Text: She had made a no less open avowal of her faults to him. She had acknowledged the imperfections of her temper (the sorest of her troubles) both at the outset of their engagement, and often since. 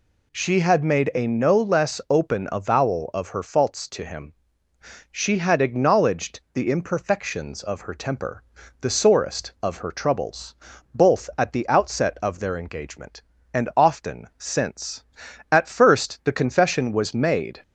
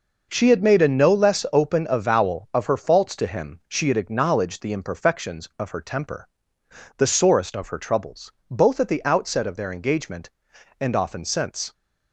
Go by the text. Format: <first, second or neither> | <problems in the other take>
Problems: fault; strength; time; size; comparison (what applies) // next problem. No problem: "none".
second | goes on to say "At first the confession was made"; strong; from 15.5 s on; 2.1 s long